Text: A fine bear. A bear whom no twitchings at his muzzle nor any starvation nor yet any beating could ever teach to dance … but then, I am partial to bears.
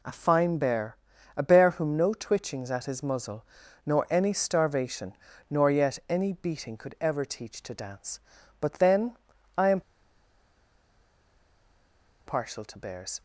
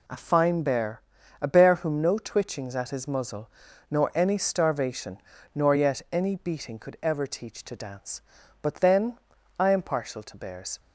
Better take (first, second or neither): second